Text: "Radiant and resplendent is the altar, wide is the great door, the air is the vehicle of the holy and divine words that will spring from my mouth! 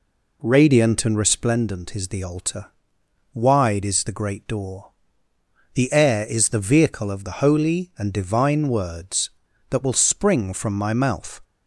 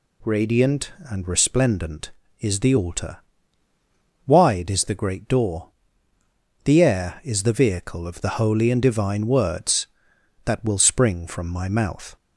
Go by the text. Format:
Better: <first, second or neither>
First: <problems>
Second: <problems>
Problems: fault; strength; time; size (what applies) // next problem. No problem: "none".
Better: second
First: starts louder than the rest; slight; until 1.7 s; 3 dB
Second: none